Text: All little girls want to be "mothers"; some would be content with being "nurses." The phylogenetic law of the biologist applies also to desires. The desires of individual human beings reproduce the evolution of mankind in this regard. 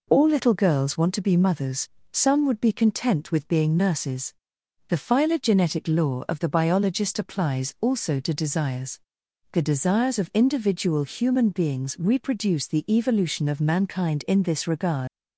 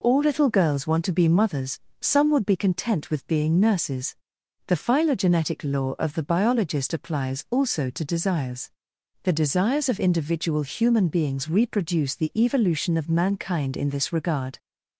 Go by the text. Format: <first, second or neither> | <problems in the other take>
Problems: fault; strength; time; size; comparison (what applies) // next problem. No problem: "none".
second | leaves "regard" unfinished; at 15.0 s; 100 ms